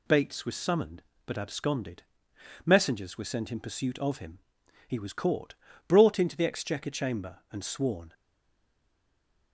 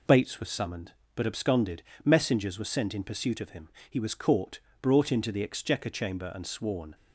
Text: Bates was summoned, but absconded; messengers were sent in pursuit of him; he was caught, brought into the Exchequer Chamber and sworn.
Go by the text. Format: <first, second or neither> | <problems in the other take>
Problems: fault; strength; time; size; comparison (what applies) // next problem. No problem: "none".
second | stays silent after the last word; noticeable; from 8.1 s on; 1.4 s long